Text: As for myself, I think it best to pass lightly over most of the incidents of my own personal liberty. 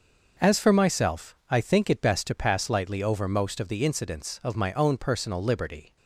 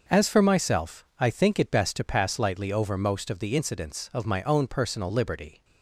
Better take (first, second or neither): neither